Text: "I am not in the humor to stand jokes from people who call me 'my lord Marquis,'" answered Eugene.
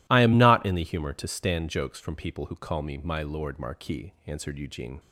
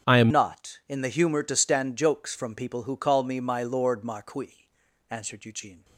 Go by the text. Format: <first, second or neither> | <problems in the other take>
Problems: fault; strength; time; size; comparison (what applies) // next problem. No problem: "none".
first | starts louder than the rest; strong; until 1.1 s; 8 dB // changes voice at "not"; from 0.3 s on; 5.5 s long